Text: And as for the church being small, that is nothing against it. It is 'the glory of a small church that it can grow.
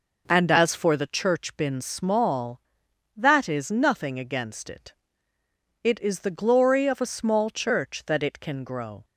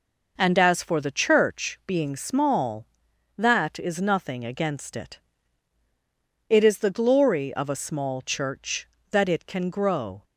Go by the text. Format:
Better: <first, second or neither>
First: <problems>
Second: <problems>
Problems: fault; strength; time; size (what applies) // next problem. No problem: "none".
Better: second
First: says "been" for "being"; at 1.5 s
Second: none